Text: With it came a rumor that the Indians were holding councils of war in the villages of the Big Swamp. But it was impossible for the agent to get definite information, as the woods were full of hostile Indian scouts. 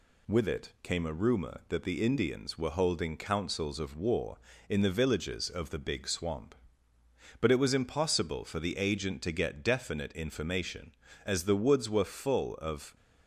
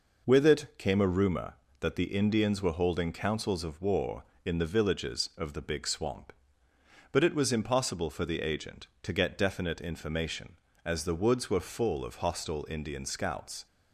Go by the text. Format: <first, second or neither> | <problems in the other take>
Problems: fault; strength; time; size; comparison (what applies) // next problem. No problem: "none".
second | stops before "hostile Indian scouts"; at 12.9 s